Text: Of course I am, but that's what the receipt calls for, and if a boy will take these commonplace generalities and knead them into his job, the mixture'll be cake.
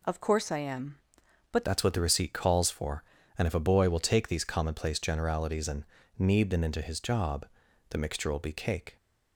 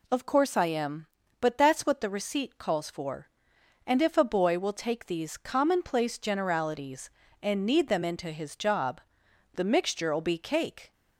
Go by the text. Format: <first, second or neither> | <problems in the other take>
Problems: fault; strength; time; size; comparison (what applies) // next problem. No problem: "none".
second | changes voice at "that's"; from 1.6 s on; 7.3 s long // pauses between "and" and "knead"; slight; at 5.8 s; 0.34 s long